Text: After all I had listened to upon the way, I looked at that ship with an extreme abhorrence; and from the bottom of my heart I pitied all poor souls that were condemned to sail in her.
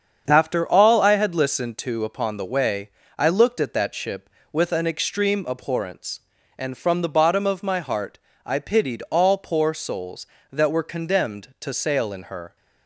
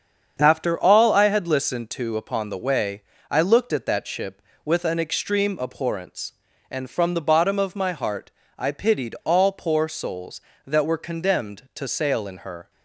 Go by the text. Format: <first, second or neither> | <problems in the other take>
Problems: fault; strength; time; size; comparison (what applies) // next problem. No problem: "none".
neither | starts louder than the rest; strong; the same in both // pauses between "heart" and "I"; slight; the same in both